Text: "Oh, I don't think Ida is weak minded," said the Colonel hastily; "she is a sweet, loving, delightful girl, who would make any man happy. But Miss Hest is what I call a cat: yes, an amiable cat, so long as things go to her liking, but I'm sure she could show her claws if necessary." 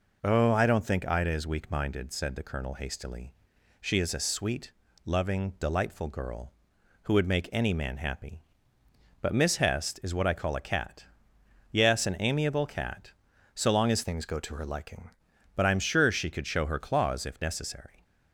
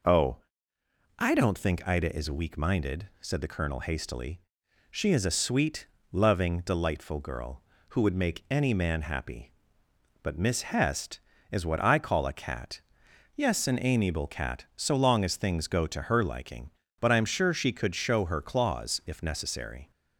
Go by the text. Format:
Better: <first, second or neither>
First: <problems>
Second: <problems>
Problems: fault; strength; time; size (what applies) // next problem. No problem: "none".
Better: second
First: changes voice from "things" to "liking"; from 14.0 to 15.1 s; 1.1 s long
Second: none